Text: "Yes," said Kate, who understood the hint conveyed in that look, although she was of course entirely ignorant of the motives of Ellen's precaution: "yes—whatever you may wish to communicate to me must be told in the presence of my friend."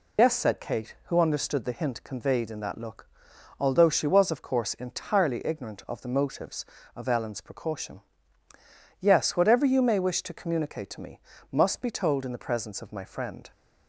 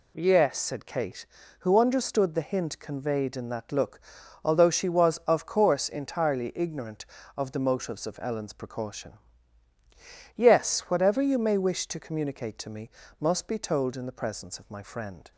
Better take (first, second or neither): second